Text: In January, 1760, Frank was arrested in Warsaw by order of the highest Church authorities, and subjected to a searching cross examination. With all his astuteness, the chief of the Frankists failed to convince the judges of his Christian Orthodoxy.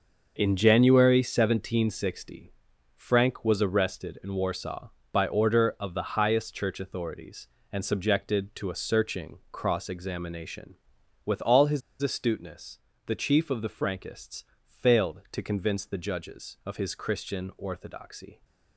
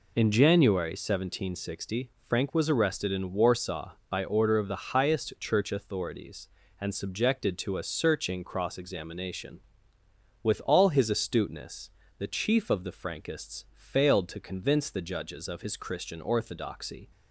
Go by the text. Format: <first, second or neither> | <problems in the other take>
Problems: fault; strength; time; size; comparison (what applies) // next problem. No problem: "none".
second | pauses between "his" and "astuteness"; slight; at 11.8 s; 0.20 s long // pauses between "Frankists" and "failed"; slight; at 14.4 s; 0.22 s long